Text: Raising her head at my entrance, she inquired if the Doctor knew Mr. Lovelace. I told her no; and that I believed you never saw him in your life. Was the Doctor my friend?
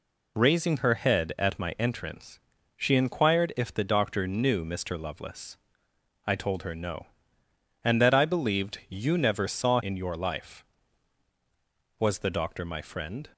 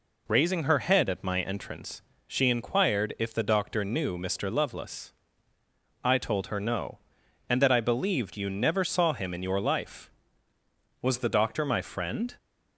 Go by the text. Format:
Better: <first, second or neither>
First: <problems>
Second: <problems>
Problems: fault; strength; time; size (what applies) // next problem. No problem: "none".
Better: second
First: skips "him"; at 9.8 s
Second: none